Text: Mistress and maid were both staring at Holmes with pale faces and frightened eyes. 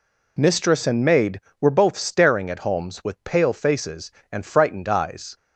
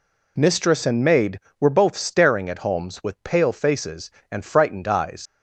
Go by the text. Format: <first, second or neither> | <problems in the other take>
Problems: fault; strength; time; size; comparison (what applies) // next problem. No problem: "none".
first | leaves "eyes" unfinished; at 5.2 s; 90 ms